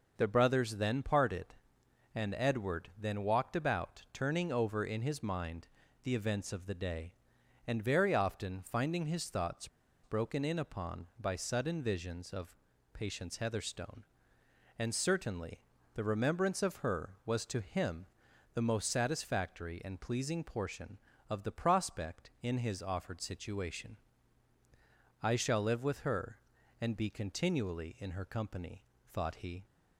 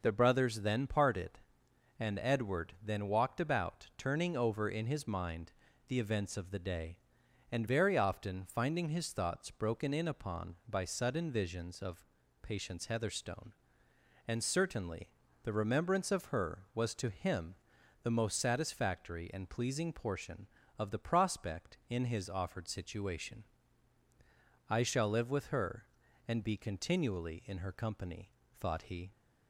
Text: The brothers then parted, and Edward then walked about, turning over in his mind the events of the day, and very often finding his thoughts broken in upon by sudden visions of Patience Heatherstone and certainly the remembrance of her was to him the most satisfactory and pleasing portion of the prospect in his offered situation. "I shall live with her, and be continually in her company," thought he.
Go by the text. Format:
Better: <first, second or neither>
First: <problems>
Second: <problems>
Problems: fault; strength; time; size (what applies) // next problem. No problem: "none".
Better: second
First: pauses between "mind" and "the"; slight; at 5.6 s; 0.36 s long // pauses between "thoughts" and "broken"; at 9.6 s; 0.36 s long // pauses between "of" and "Patience"; at 12.5 s; 0.38 s long // pauses between "certainly" and "the"; slight; at 15.5 s; 0.34 s long // pauses between "him" and "the"; noticeable; at 18.0 s; 0.48 s long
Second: pauses between "mind" and "the"; slight; at 5.5 s; 0.36 s long // pauses between "of" and "Patience"; at 12.0 s; 0.38 s long // pauses between "certainly" and "the"; slight; at 15.0 s; 0.34 s long // pauses between "him" and "the"; noticeable; at 17.5 s; 0.48 s long